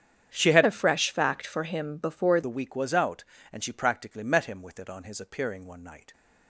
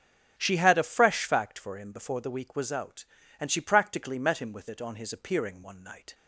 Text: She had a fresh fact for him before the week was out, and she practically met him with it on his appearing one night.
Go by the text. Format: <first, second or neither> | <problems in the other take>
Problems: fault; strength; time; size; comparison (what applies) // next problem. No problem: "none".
second | starts louder than the rest; strong; until 1.3 s; 9 dB; also in the second // changes voice from "a" to "before"; from 0.6 to 2.4 s; 1.8 s long